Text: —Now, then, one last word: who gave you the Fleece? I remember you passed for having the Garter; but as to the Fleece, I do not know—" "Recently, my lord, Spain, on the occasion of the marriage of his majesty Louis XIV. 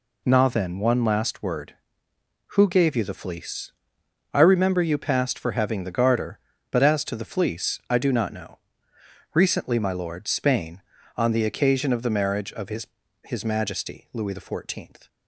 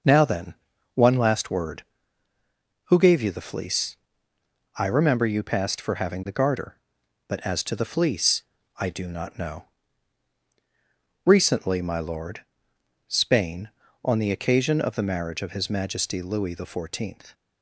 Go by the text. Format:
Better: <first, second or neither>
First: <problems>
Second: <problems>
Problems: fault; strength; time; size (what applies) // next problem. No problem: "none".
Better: second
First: says "his" twice; at 13.2 s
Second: none